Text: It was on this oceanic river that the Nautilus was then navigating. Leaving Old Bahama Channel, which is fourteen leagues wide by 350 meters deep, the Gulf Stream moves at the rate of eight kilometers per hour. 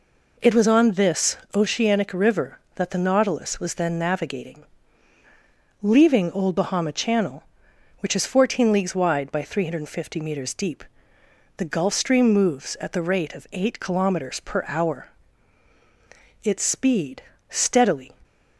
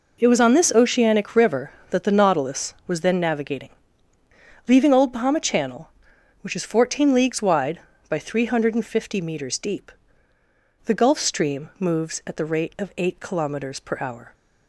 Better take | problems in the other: second | pauses between "this" and "oceanic"; slight; at 1.3 s; 0.20 s long // goes on to say "Its speed steadily"; strong; from 16.4 s on; 1.6 s long

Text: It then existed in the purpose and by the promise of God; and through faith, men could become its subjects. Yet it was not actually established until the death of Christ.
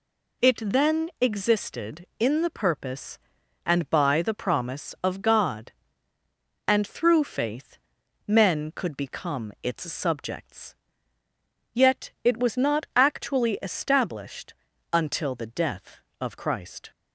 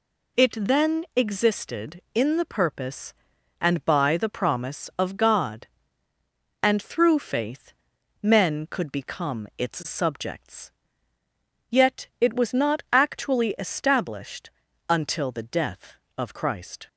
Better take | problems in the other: neither | pauses between "established" and "until"; the same in both

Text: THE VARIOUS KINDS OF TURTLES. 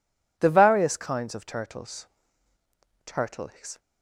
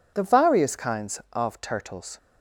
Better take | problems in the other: second | says "TURTLES" twice; at 3.0 s

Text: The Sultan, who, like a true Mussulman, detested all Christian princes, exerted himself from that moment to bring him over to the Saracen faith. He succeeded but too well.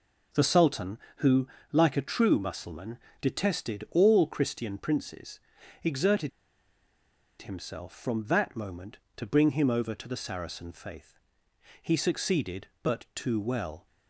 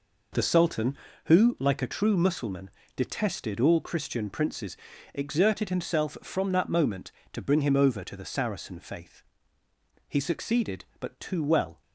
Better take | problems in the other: second | pauses between "exerted" and "himself"; at 6.3 s; 1.1 s long

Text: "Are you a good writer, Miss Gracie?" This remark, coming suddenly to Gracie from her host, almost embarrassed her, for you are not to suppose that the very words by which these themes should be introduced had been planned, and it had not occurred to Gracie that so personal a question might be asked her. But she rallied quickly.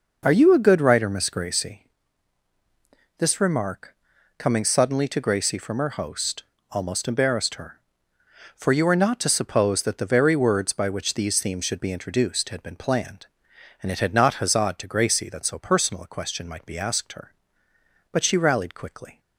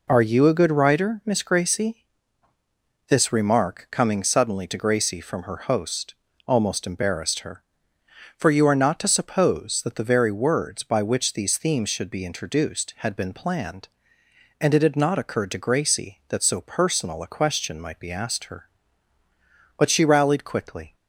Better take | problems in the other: second | says "huzzaed" for "occurred"; at 14.3 s

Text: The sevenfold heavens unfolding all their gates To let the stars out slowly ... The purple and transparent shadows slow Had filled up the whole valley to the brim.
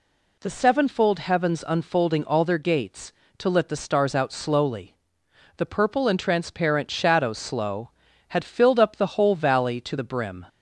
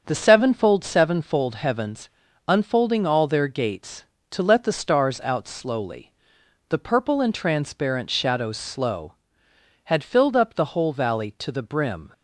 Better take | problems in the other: first | starts louder than the rest; until 1.0 s; 7 dB // says "sevenfold" twice; at 0.8 s // pauses between "heavens" and "unfolding"; at 2.0 s; 0.38 s long

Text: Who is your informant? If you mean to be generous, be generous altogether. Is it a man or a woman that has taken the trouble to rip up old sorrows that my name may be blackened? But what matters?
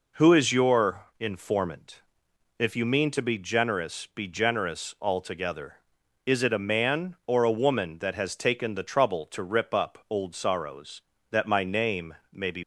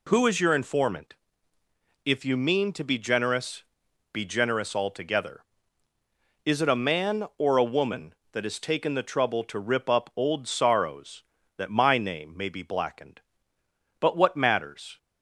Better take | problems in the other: second | pauses between "name" and "may"; slight; at 12.1 s; 0.18 s long // stops before "blackened But what matters"; at 12.6 s

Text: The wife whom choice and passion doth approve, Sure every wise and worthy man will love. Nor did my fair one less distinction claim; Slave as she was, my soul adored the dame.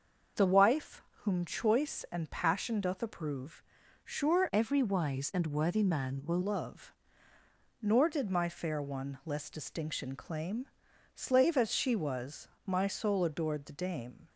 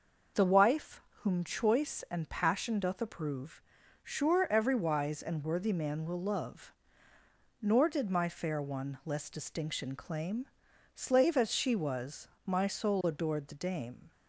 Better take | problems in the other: second | starts louder than the rest; until 1.5 s; 6 dB // pauses between "wife" and "whom"; slight; at 1.0 s; 0.20 s long; slight in the second // changes voice from "every" to "will"; from 4.5 to 6.3 s; 1.8 s long

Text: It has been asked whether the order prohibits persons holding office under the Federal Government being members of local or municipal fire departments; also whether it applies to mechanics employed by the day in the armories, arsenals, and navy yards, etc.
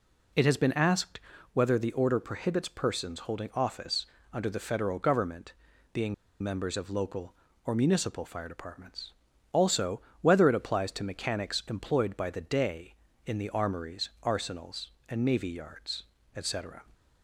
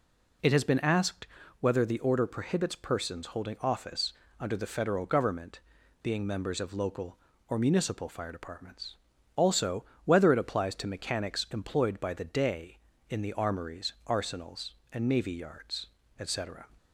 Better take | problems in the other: second | pauses between "asked" and "whether"; slight; at 1.1 s; 0.34 s long; slight in the second // pauses between "office" and "under"; slight; at 4.0 s; 0.28 s long; slight in the second // pauses between "Government" and "being"; at 5.5 s; 0.40 s long; also in the second // pauses between "being" and "members"; slight; at 6.1 s; 0.28 s long // pauses between "also" and "whether"; slight; at 10.0 s; 0.22 s long; slight in the second

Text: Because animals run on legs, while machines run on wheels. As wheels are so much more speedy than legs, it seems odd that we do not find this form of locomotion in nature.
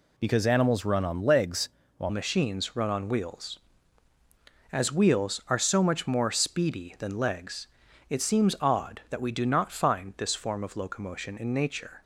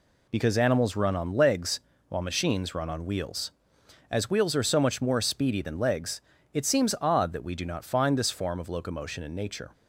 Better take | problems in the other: second | changes voice at "machines"; from 2.1 s on; 9.9 s long

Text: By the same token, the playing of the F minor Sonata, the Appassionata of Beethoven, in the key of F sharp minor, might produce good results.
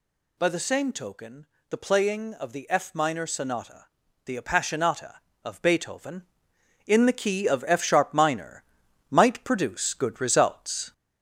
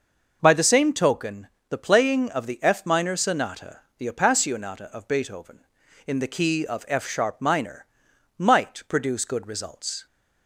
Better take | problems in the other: second | gets louder; throughout; 3.5 dB

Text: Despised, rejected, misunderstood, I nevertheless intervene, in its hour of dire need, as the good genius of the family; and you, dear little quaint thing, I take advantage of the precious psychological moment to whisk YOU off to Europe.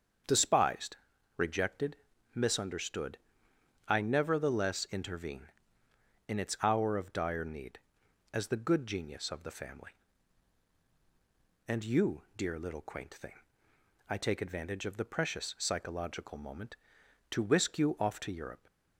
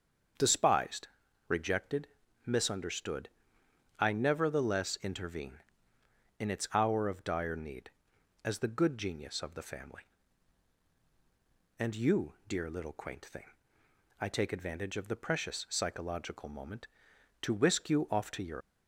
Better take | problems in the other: first | starts louder than the rest; strong; until 1.7 s; 7.5 dB; strong in the first // leaves "Europe" unfinished; at 18.6 s; 165 ms

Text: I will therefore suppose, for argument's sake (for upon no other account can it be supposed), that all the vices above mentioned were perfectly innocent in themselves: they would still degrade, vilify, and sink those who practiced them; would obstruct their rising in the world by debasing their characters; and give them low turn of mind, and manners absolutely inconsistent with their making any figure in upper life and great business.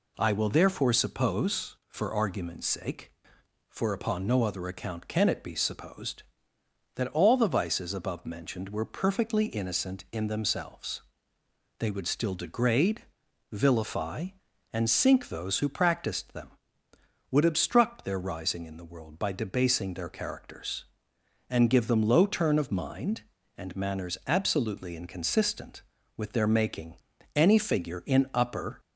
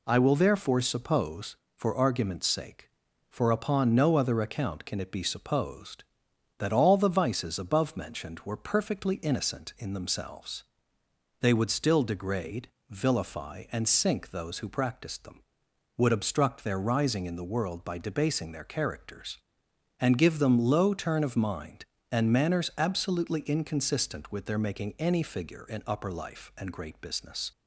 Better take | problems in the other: second | pauses between "making" and "any"; at 26.9 s; 0.42 s long // stops before "life and great business"; at 28.7 s

